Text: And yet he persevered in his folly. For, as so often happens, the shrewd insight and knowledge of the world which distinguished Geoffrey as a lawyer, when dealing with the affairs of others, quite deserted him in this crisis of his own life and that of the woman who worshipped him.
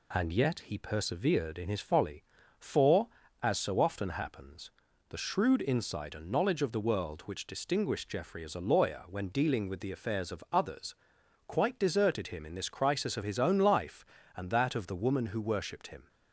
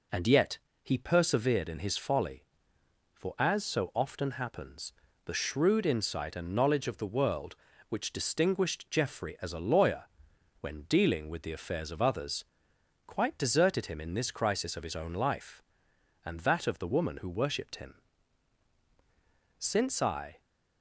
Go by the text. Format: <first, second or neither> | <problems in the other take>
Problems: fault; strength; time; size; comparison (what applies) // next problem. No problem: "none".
first | pauses between "yet" and "he"; slight; at 0.5 s; 0.26 s long // goes on to say "Since I"; noticeable; from 19.5 s on; 0.82 s long